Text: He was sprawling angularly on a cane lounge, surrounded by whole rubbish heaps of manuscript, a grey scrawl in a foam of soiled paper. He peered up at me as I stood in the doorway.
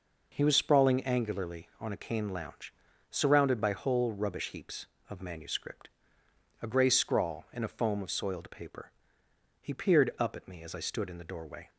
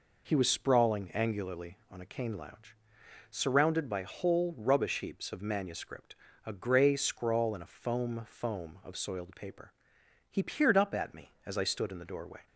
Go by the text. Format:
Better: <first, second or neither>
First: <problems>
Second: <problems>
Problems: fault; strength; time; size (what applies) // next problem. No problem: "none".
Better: first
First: none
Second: says "foam" twice; at 8.2 s